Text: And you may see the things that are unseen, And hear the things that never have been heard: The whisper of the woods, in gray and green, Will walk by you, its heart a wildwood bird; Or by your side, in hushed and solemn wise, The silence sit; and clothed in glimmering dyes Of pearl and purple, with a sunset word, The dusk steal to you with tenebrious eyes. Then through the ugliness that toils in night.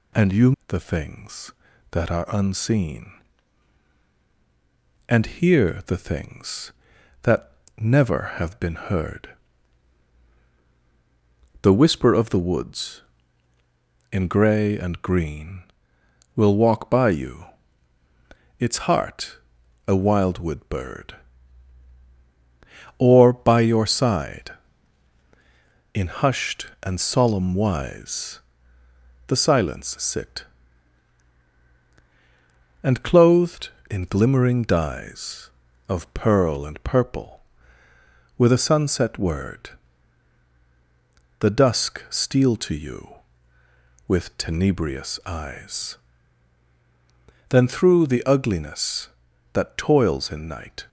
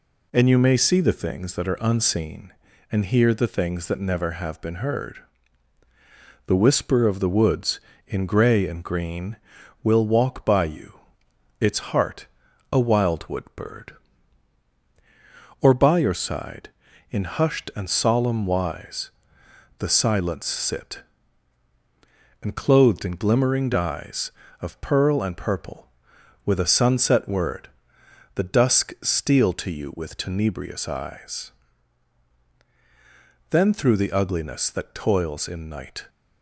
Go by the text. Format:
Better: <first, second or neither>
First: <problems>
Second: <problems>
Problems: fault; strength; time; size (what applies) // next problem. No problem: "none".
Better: second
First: skips "may see"; at 0.5 s // pauses between "that" and "never"; slight; at 7.5 s; 0.26 s long // pauses between "heart" and "a"; noticeable; at 19.3 s; 0.50 s long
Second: pauses between "heart" and "a"; noticeable; at 12.2 s; 0.46 s long